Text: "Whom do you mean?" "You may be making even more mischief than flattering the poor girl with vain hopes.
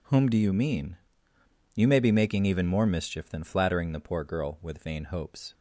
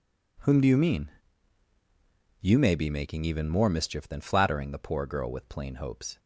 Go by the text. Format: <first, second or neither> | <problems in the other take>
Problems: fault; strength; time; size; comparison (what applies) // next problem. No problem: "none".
first | says "plain" for "vain"; at 5.4 s